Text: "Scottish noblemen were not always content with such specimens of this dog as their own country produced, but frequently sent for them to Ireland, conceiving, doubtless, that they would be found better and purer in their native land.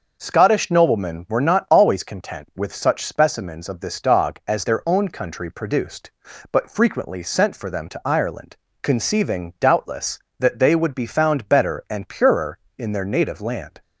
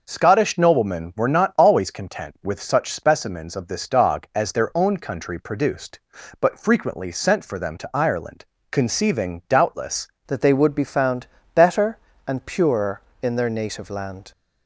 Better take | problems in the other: first | changes voice at "that"; from 10.2 s on; 4.1 s long // pauses between "found" and "better"; slight; at 11.2 s; 0.28 s long

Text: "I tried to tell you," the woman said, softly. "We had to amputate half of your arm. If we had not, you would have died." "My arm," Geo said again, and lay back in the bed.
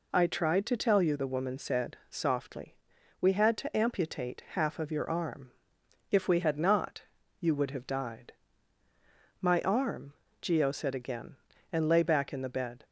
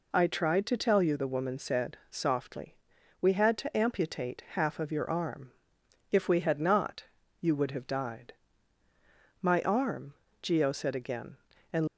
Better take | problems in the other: first | stops before "lay back in the bed"; at 11.8 s

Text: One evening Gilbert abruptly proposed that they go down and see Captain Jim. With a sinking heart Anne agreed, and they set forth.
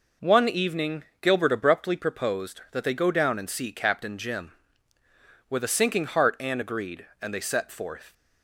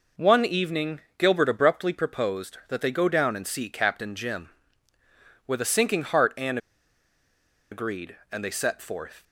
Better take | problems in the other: first | pauses between "evening" and "Gilbert"; slight; at 0.9 s; 0.16 s long; slight in the first // pauses between "Anne" and "agreed"; at 6.5 s; 1.1 s long

